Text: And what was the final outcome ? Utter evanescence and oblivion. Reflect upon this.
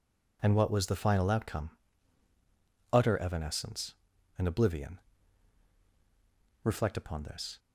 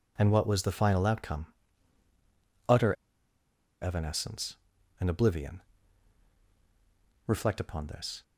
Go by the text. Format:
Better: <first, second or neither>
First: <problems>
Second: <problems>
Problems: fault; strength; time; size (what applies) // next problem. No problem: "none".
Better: first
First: none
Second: pauses between "Utter" and "evanescence"; noticeable; at 2.9 s; 0.87 s long